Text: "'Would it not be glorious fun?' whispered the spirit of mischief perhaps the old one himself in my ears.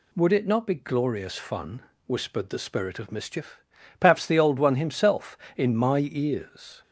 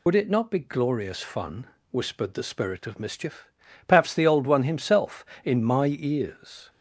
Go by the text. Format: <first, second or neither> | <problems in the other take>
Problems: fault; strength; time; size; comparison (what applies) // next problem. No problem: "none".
first | loses the start of "Would"; at 0.0 s; 100 ms // pauses between "mischief" and "perhaps"; at 3.4 s; 0.40 s long; also in the first